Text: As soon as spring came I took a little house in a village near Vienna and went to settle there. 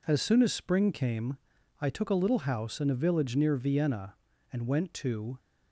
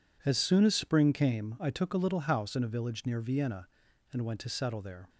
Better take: second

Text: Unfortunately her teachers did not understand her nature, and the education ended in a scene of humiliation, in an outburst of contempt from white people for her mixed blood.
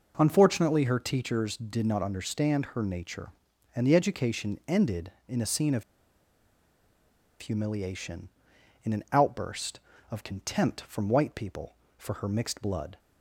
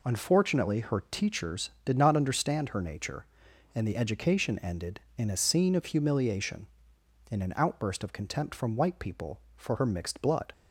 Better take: second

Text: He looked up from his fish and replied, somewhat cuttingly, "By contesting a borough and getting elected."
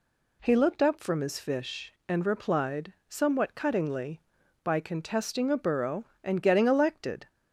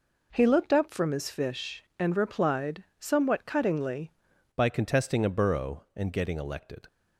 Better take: first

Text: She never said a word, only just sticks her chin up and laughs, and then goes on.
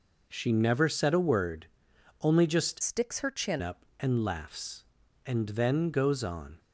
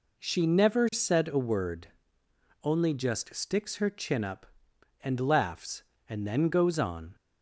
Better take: second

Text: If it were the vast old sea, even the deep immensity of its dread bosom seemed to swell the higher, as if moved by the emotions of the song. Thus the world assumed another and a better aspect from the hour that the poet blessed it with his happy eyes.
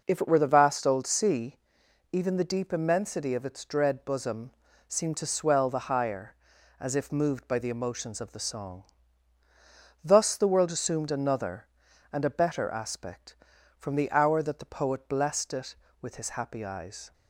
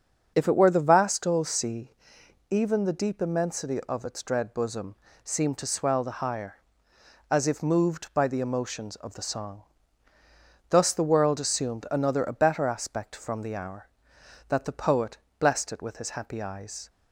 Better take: first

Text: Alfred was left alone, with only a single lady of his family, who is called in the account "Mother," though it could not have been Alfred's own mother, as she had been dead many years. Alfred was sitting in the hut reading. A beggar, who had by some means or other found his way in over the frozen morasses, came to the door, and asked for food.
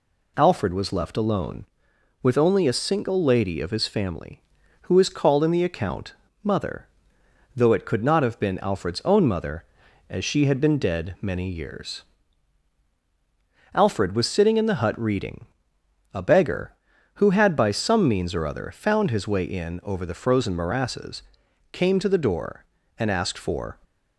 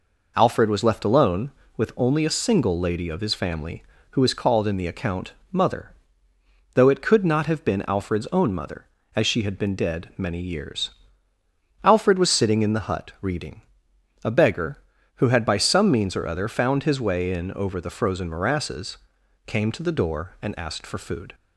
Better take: second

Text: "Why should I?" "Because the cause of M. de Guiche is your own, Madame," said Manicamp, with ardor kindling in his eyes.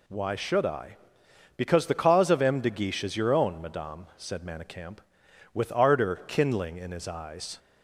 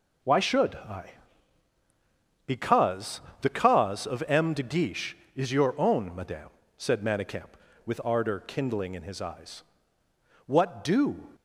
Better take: first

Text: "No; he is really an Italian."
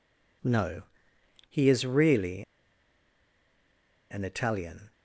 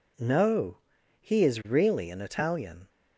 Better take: second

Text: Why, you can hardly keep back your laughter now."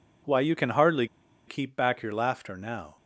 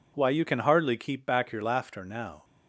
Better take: second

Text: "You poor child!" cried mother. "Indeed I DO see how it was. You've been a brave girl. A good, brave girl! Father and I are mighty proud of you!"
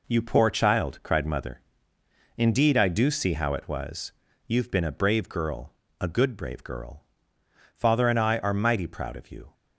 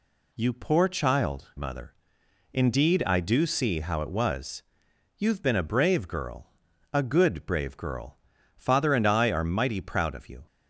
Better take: first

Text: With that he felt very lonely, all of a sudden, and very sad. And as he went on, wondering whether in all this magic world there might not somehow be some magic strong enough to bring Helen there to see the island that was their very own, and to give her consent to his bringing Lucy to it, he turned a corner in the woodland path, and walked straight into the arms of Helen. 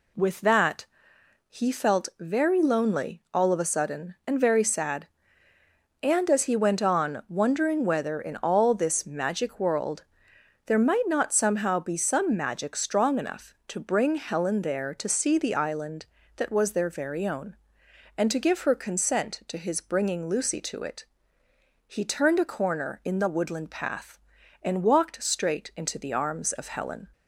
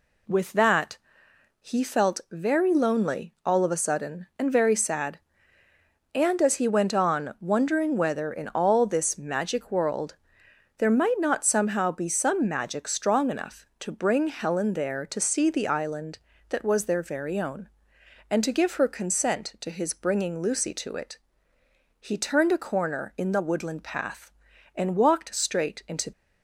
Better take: first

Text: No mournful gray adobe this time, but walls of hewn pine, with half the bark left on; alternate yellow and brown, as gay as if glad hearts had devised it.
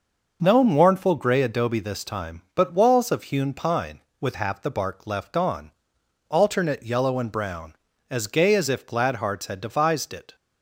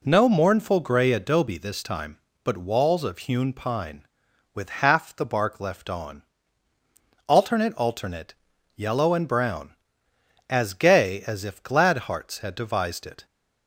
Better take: first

